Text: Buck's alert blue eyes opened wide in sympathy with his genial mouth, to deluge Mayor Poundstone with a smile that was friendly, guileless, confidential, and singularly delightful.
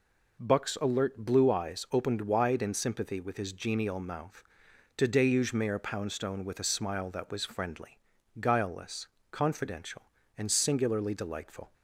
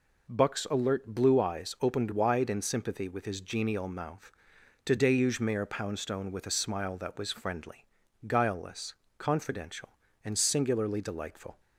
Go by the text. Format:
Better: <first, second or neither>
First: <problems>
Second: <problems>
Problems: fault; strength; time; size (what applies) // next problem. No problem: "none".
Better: neither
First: none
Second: none